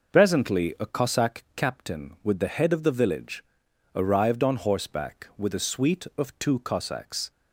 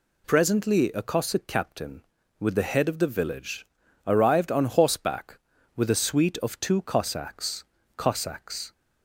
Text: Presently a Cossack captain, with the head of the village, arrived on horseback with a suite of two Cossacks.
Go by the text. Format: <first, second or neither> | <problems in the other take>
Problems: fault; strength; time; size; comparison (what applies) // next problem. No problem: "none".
first | says "Cossacks" twice; at 7.9 s